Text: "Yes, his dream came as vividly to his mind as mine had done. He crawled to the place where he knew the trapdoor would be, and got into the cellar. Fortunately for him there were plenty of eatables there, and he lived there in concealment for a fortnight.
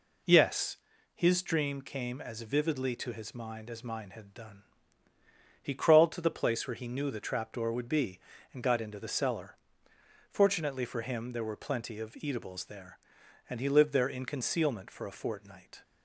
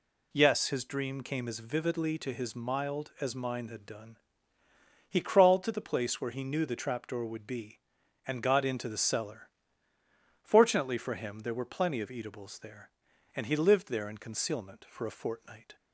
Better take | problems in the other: first | says "mild" for "mind"; at 2.5 s

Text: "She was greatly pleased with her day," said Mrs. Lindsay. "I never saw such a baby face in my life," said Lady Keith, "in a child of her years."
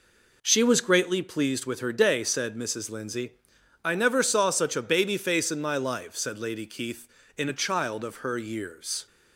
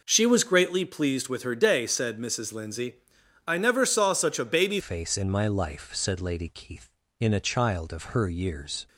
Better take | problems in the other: first | changes voice at "face"; from 4.7 s on; 4.1 s long

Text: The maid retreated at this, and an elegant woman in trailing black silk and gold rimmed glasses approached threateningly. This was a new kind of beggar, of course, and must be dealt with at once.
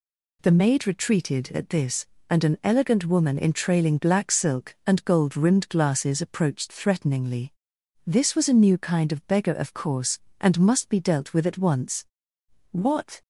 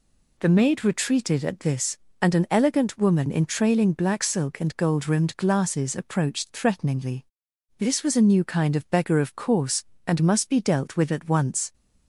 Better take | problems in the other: second | goes on to say "What"; from 12.6 s on; 0.52 s long

